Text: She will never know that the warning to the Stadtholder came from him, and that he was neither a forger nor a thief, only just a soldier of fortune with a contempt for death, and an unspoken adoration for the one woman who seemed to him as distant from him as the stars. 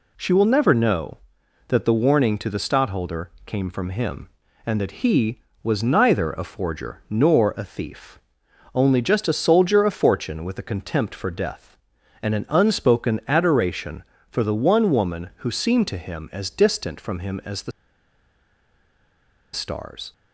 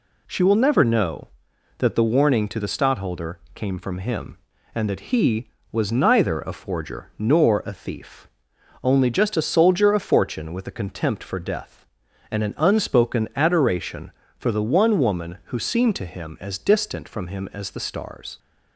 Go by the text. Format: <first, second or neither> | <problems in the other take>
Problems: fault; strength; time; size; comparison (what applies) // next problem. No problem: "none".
second | pauses between "the" and "stars"; strong; at 17.7 s; 1.8 s long